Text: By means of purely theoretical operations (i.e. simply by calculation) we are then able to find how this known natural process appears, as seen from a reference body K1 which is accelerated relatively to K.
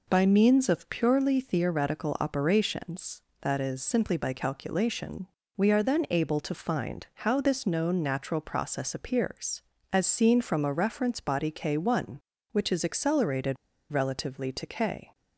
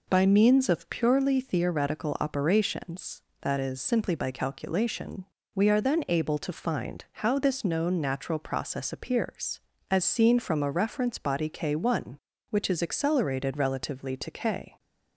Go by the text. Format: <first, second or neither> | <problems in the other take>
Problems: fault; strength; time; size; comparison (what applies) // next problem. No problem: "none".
second | pauses between "accelerated" and "relatively"; slight; at 13.5 s; 0.35 s long